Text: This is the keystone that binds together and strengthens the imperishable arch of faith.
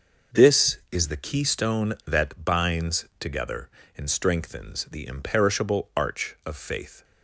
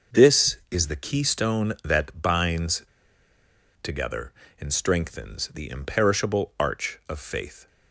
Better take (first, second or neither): first